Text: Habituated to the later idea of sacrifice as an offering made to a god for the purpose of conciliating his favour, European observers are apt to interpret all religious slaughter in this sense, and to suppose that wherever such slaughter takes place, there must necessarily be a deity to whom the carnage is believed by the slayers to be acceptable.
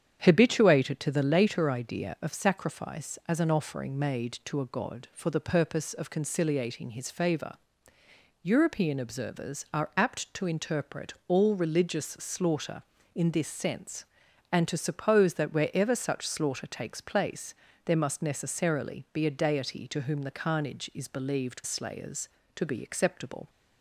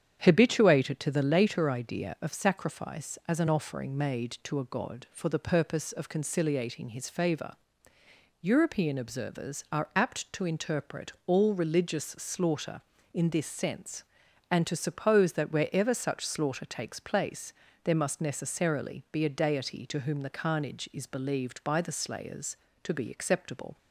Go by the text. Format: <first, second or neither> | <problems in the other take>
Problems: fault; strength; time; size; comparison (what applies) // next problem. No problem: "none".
second | starts louder than the rest; strong; until 1.2 s; 8.5 dB; strong in the second // skips "by the"; at 21.6 s